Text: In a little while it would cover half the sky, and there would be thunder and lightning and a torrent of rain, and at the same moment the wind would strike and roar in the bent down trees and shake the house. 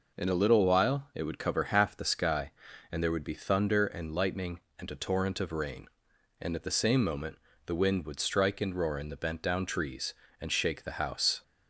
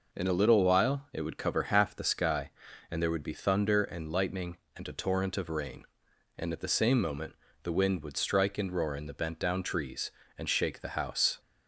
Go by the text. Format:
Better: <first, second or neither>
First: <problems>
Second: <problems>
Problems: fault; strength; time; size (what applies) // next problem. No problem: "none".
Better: neither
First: pauses between "moment" and "the"; slight; at 7.3 s; 0.28 s long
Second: pauses between "moment" and "the"; slight; at 7.3 s; 0.28 s long